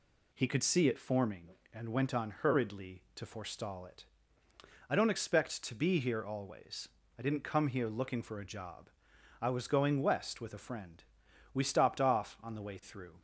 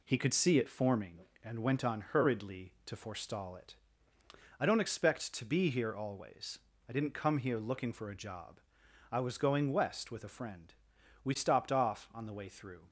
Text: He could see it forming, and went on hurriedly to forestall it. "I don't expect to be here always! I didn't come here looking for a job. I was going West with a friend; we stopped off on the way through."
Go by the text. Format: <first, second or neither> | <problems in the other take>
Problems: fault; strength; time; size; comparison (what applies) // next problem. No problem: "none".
first | gets quieter; noticeable; throughout; 4.5 dB